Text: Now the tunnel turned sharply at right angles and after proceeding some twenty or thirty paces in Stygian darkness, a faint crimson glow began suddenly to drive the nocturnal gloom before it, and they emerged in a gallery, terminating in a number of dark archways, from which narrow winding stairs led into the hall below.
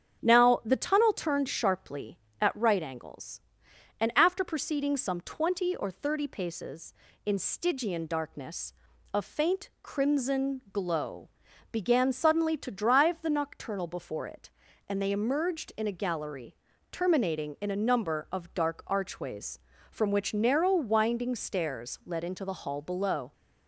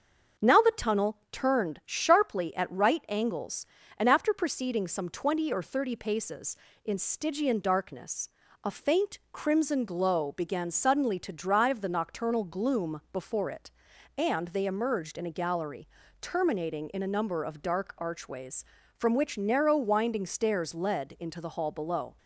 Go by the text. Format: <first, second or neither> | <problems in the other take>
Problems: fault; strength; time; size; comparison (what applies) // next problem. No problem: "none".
second | starts louder than the rest; strong; until 1.2 s; 8 dB; also in the second // pauses between "glow" and "began"; at 11.2 s; 0.42 s long // skips "gloom"; at 13.8 s